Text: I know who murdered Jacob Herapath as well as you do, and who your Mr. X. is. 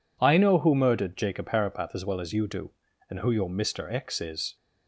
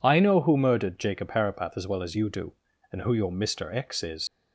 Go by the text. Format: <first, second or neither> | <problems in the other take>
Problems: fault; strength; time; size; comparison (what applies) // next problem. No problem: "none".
first | leaves "is" unfinished; at 4.2 s; 110 ms